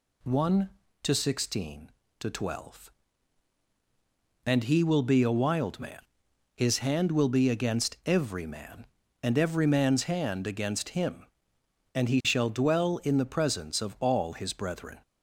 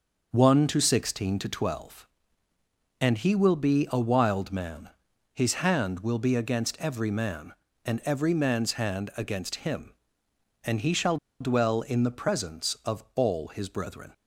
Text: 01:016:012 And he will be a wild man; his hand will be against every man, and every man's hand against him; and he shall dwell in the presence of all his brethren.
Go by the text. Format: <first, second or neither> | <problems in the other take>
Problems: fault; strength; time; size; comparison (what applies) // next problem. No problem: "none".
first | starts louder than the rest; until 1.3 s; 6 dB // pauses between "shall" and "dwell"; slight; at 11.1 s; 0.23 s long